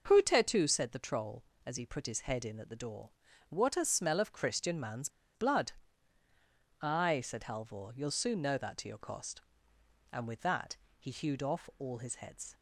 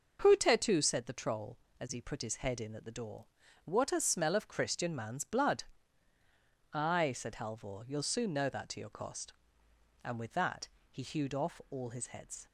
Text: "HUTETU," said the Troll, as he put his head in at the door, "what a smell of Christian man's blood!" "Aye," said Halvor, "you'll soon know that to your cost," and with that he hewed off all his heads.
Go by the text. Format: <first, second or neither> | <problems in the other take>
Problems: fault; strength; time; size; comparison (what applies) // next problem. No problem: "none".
second | pauses between "man's" and "blood"; slight; at 5.0 s; 0.26 s long // pauses between "that" and "he"; slight; at 10.7 s; 0.24 s long; slight in the second